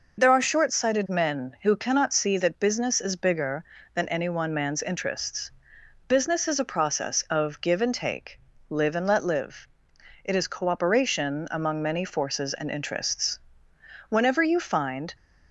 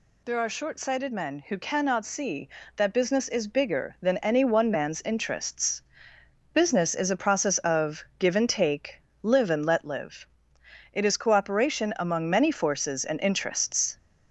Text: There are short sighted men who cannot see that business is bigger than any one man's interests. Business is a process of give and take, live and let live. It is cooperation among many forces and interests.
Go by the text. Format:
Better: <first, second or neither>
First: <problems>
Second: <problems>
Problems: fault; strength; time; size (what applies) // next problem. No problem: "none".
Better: second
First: goes on to say "Whenever you find"; noticeable; from 14.1 s on; 1.0 s long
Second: none